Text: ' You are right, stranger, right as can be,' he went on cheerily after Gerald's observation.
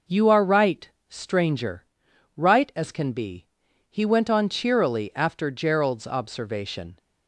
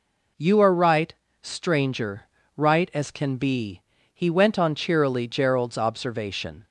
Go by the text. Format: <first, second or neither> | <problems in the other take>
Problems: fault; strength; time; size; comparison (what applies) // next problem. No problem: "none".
first | skips "after"; at 5.2 s